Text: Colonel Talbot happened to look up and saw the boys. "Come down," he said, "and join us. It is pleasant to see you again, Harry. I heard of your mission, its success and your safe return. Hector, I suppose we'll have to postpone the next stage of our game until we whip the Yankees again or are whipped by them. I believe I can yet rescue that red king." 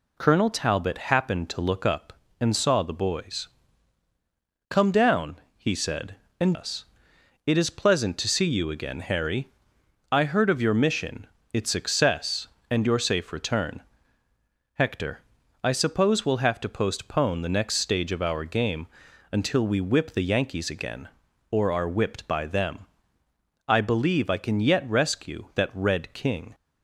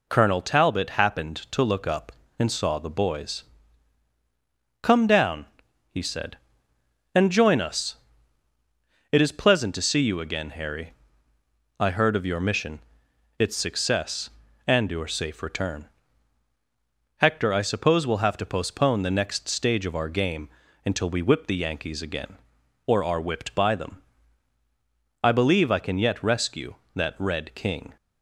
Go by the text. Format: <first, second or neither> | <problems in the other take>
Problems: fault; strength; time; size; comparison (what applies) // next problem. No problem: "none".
second | skips "join"; at 6.5 s // pauses between "game" and "until"; noticeable; at 18.8 s; 0.46 s long; slight in the second